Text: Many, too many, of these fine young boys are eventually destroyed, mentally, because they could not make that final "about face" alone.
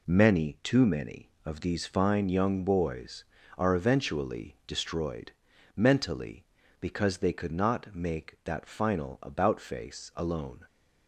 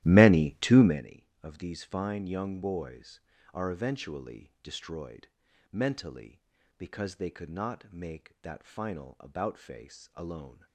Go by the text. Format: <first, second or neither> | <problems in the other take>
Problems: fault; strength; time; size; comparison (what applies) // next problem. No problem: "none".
first | starts louder than the rest; strong; until 1.0 s; 14.5 dB